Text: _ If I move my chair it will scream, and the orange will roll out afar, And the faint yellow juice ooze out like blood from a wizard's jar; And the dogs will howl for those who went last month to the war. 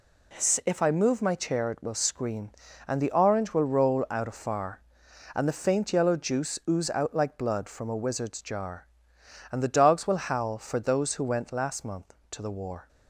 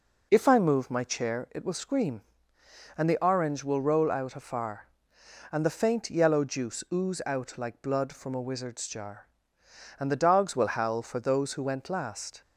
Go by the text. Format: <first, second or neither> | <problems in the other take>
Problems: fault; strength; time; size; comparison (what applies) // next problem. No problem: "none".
first | stops before "month to the war"; at 12.4 s